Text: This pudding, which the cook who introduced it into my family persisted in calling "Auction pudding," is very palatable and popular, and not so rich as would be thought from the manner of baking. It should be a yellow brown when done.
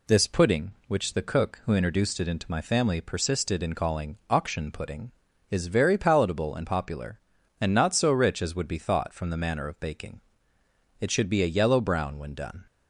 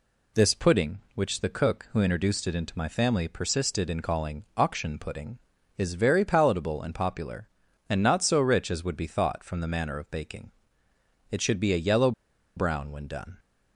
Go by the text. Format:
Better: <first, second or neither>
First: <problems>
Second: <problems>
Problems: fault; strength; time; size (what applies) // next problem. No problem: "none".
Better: first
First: none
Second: pauses between "yellow" and "brown"; at 12.1 s; 0.45 s long